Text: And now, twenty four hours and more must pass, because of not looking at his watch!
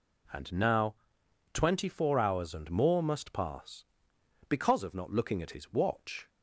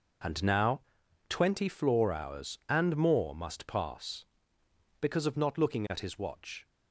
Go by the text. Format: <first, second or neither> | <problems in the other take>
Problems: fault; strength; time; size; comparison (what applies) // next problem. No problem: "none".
first | says "floor" for "four"; at 1.6 s